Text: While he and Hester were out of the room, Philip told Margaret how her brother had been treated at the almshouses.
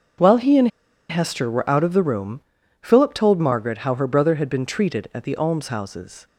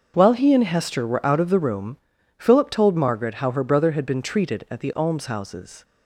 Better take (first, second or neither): second